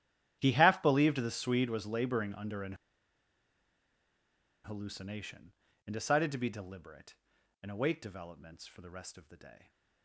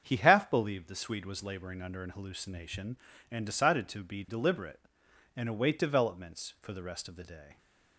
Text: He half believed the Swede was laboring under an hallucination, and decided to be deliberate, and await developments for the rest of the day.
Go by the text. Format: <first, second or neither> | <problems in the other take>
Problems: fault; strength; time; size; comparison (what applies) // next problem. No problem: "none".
second | starts louder than the rest; strong; until 1.4 s; 11.5 dB; strong in the second // pauses between "an" and "hallucination"; strong; at 2.7 s; 1.9 s long